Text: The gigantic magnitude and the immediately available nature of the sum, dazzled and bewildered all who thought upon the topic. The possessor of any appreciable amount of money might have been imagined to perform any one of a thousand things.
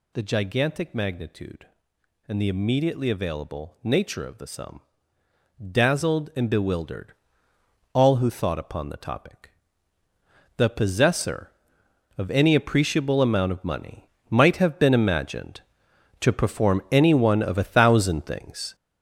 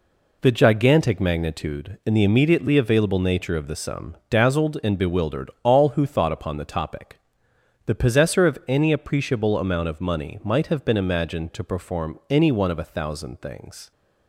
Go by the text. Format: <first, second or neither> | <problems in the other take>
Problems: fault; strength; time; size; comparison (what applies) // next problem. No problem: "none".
second | gets louder; strong; throughout; 7.5 dB // pauses between "bewildered" and "all"; noticeable; at 7.1 s; 0.80 s long // pauses between "money" and "might"; slight; at 14.0 s; 0.20 s long